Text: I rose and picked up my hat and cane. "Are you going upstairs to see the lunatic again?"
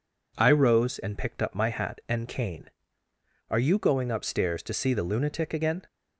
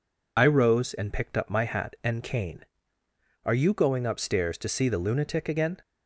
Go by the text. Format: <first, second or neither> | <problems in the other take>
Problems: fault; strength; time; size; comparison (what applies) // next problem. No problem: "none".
first | loses the start of "I"; at 0.3 s; 65 ms